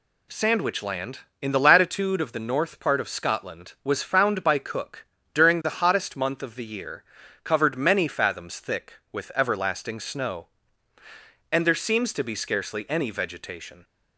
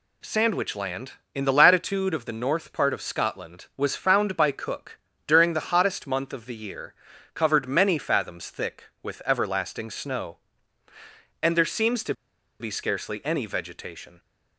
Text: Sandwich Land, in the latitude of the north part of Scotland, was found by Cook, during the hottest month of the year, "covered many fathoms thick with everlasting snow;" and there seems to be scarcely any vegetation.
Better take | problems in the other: first | pauses between "to" and "be"; noticeable; at 12.1 s; 0.45 s long

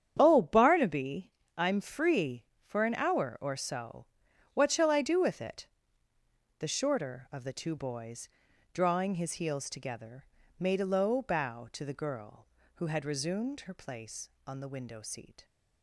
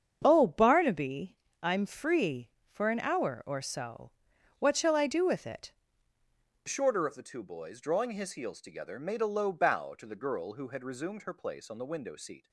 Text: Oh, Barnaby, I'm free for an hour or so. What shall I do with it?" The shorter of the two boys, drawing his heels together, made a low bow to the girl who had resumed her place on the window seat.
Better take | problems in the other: first | starts louder than the rest; strong; until 1.2 s; 7.5 dB; strong in the first // changes voice at "shorter"; from 6.6 s on; 5.8 s long

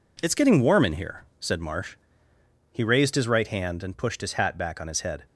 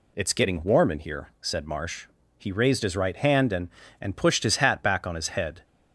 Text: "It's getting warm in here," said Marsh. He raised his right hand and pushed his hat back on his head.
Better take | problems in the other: first | says "and" twice; at 3.9 s

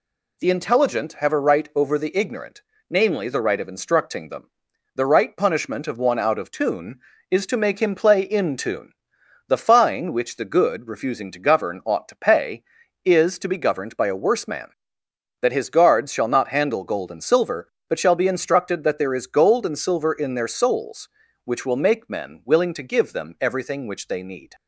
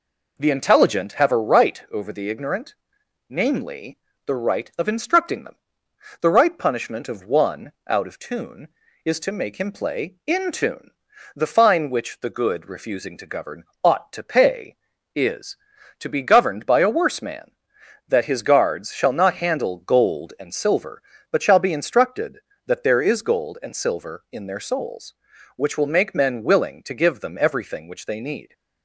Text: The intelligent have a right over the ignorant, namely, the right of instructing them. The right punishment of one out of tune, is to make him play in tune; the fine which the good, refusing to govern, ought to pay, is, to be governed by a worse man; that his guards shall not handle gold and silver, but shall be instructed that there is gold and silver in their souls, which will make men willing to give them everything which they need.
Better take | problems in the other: neither | none

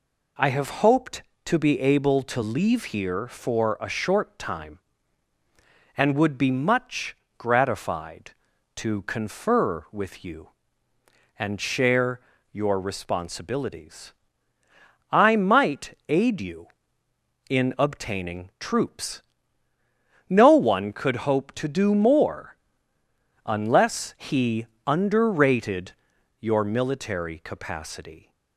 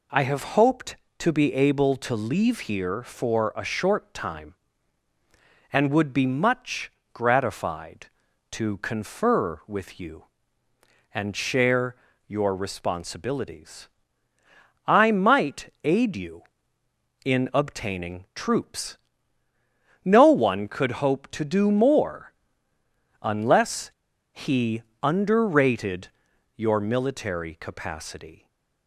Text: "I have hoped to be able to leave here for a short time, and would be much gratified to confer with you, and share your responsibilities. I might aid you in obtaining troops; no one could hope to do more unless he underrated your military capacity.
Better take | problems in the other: first | pauses between "much" and "gratified"; slight; at 6.8 s; 0.24 s long; slight in the first // pauses between "share" and "your"; slight; at 11.9 s; 0.32 s long; slight in the first // pauses between "more" and "unless"; noticeable; at 22.3 s; 0.90 s long; noticeable in the first // pauses between "unless" and "he"; at 23.9 s; 0.41 s long // pauses between "he" and "underrated"; slight; at 24.8 s; 0.22 s long; slight in the first // pauses between "underrated" and "your"; noticeable; at 26.0 s; 0.48 s long; noticeable in the first // stays silent after the last word; slight; from 28.3 s on; 0.5 s long

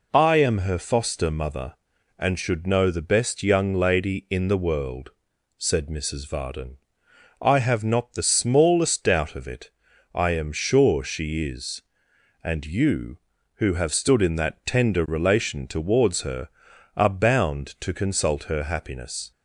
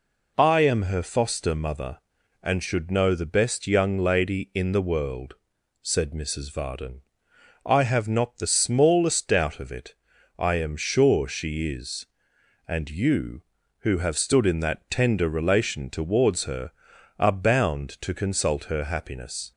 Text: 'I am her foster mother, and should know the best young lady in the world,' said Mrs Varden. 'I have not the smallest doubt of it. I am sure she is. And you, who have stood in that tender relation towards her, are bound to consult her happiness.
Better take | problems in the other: neither | none

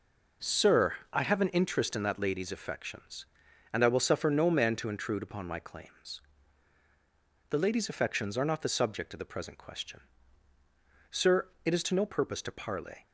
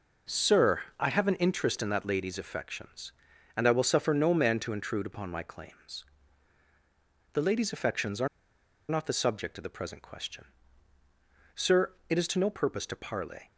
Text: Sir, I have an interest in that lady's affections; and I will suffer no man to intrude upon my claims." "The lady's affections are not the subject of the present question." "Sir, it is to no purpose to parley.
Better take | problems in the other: first | pauses between "are" and "not"; noticeable; at 8.2 s; 0.61 s long

